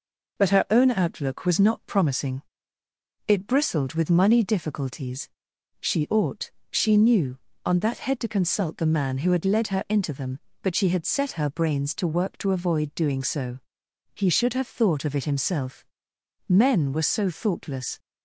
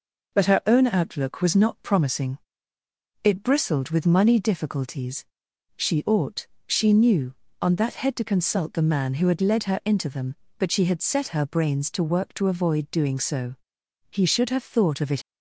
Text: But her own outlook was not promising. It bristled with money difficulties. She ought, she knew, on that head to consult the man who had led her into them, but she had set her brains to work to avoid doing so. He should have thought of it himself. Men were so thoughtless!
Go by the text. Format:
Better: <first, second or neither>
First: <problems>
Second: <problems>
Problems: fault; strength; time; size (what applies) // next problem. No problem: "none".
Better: first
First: none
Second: stops before "himself Men were so thoughtless"; at 15.2 s